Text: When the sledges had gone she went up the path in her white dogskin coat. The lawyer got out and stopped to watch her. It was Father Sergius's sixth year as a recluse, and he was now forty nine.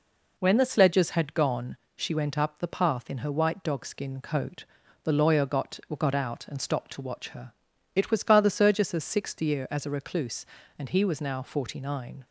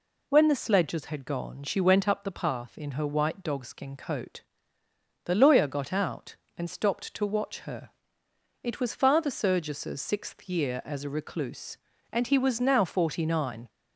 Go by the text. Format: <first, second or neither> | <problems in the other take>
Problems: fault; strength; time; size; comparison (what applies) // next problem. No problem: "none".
second | pauses between "gone" and "she"; slight; at 1.7 s; 0.18 s long // says "got" twice; at 5.9 s